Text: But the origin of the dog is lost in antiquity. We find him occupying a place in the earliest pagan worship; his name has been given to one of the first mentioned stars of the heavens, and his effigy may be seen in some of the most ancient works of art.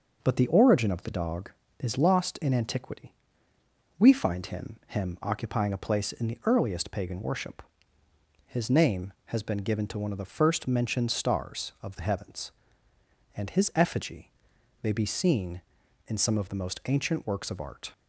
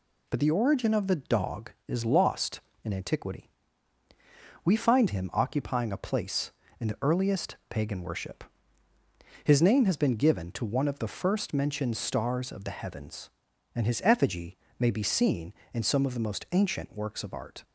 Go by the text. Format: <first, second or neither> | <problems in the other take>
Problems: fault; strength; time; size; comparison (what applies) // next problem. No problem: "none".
second | says "him" twice; at 4.8 s // pauses between "effigy" and "may"; noticeable; at 14.3 s; 0.52 s long; slight in the second